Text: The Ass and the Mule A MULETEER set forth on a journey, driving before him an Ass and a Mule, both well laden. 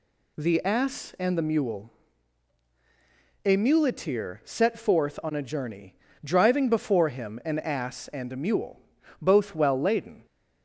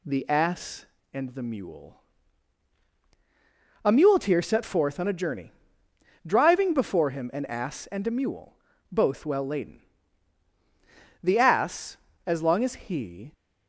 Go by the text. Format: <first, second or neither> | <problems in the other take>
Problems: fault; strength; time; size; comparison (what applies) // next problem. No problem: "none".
first | pauses between "Mule" and "A"; strong; at 1.9 s; 1.8 s long; strong in the first // goes on to say "The Ass as long as he"; strong; from 11.2 s on; 2.1 s long